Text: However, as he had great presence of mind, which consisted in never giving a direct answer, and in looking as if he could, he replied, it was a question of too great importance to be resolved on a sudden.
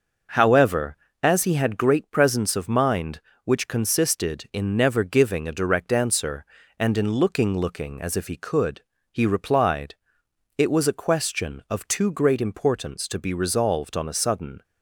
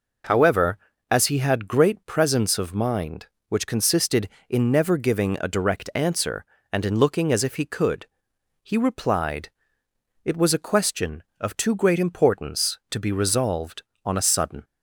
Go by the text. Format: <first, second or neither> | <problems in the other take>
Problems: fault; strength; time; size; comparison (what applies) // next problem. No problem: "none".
second | starts louder than the rest; noticeable; until 1.6 s; 6 dB // says "looking" twice; at 7.5 s